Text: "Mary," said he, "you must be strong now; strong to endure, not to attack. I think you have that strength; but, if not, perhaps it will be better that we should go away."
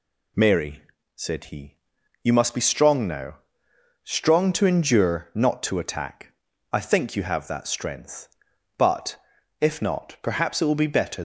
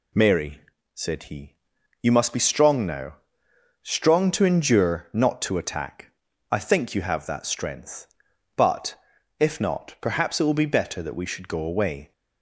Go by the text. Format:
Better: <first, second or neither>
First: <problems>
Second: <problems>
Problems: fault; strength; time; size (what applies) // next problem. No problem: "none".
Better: second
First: stops before "that we should go away"; at 11.1 s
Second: none